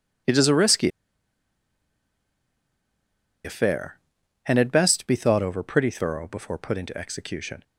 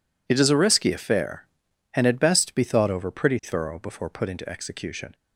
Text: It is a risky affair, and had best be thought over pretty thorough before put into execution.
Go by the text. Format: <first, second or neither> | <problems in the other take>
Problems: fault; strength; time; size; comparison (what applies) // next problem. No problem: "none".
second | pauses between "risky" and "affair"; strong; at 0.8 s; 2.5 s long